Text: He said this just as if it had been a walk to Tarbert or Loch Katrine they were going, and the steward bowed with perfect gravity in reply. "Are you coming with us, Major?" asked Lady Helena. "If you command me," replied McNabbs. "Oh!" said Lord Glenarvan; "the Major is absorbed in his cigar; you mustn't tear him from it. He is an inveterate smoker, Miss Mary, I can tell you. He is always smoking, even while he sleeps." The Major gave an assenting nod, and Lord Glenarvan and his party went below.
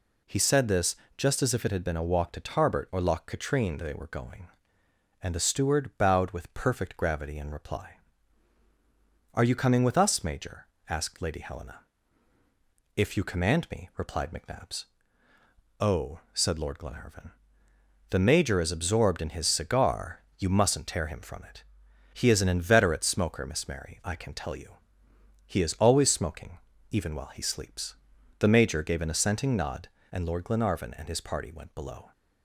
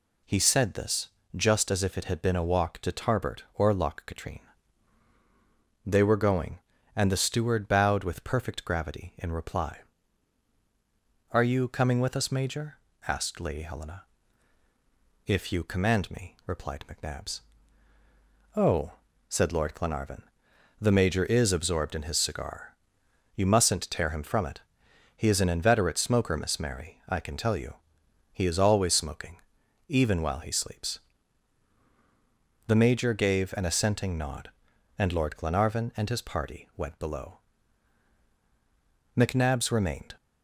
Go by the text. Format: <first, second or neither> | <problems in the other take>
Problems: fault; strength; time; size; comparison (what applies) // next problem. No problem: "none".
first | pauses between "this" and "just"; slight; at 1.0 s; 0.26 s long; slight in the first // pauses between "Katrine" and "they"; strong; at 4.3 s; 1.4 s long // goes on to say "McNabbs remained"; noticeable; from 39.1 s on; 0.96 s long